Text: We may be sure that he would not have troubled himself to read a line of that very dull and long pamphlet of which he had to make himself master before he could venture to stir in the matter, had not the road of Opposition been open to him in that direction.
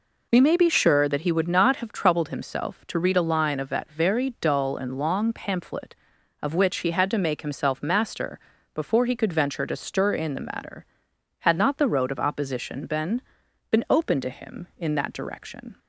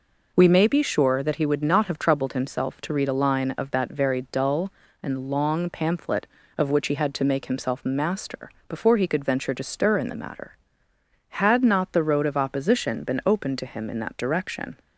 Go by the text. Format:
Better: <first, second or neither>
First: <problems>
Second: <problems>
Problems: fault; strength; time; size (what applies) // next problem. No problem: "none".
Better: second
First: pauses between "master" and "before"; slight; at 8.3 s; 0.36 s long // says "been" twice; at 13.7 s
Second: pauses between "master" and "before"; slight; at 8.4 s; 0.20 s long